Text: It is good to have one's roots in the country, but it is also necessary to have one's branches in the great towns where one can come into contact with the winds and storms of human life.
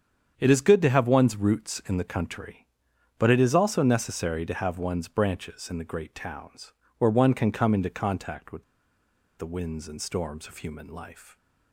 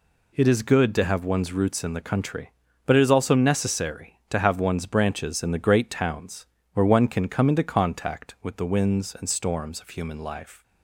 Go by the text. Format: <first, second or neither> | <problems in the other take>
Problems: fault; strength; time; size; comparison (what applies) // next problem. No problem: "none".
second | starts louder than the rest; strong; until 1.3 s; 8 dB // pauses between "towns" and "where"; slight; at 6.7 s; 0.24 s long; slight in the second // pauses between "with" and "the"; noticeable; at 8.6 s; 0.75 s long